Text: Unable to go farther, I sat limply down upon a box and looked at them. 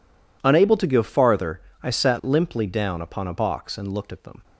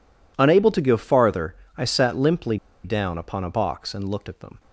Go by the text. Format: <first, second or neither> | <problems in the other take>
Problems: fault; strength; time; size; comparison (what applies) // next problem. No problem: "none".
first | pauses between "limply" and "down"; slight; at 2.5 s; 0.27 s long